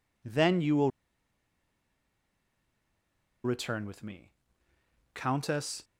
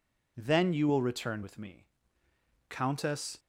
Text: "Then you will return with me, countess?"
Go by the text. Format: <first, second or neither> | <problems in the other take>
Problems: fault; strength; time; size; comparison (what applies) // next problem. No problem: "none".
second | pauses between "will" and "return"; strong; at 0.9 s; 2.5 s long